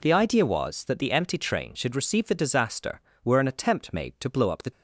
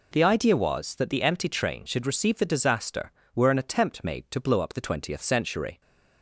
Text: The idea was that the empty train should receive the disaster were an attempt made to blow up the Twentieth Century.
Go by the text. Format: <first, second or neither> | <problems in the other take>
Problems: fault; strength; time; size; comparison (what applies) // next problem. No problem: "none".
second | stops before "Twentieth Century"; at 4.7 s